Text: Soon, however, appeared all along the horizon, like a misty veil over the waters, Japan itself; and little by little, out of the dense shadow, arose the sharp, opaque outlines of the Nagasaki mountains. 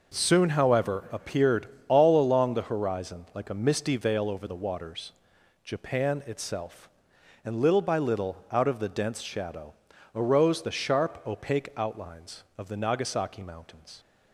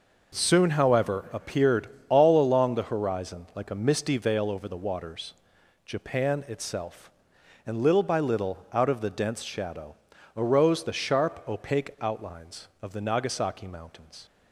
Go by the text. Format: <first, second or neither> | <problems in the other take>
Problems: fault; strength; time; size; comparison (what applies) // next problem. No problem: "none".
neither | pauses between "appeared" and "all"; slight; the same in both